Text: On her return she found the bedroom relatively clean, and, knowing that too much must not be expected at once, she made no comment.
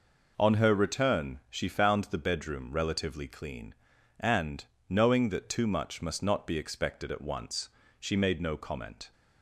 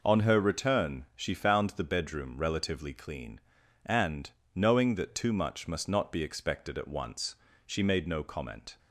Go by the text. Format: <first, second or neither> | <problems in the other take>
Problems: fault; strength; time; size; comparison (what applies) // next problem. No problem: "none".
neither | none